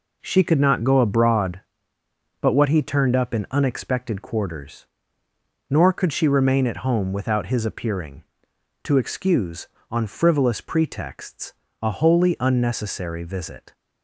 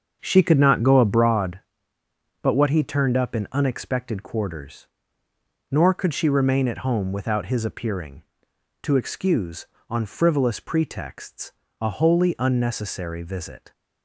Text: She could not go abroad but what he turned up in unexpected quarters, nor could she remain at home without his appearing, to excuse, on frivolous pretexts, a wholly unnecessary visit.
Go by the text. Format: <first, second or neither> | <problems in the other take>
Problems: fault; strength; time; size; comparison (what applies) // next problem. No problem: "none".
first | starts louder than the rest; until 1.3 s; 7 dB